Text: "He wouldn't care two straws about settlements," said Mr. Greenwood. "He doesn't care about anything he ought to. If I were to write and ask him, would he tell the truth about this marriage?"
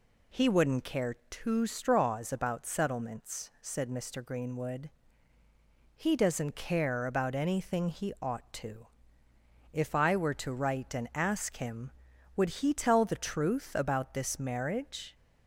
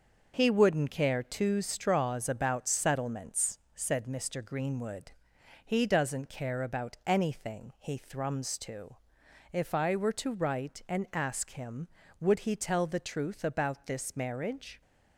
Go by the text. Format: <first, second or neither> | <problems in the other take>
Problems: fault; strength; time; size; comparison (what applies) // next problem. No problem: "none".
first | says "thrums" for "ought"; at 7.9 s